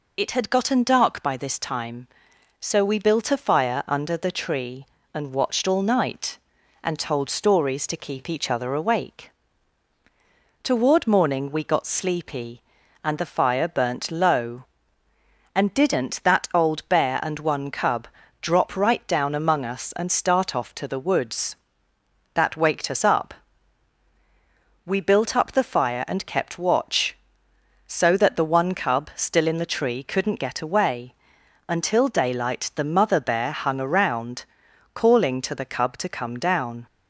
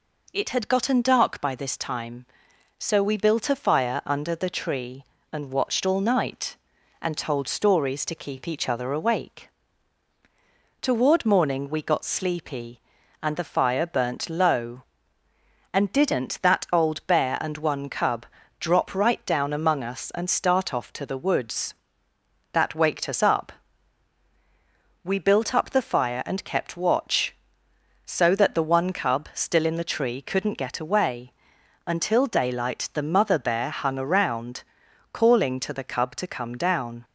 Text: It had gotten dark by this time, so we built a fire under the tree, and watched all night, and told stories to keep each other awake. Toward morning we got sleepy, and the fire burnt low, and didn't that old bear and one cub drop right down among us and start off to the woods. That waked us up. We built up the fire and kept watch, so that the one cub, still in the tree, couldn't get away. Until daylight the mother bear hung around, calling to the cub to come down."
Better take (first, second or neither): second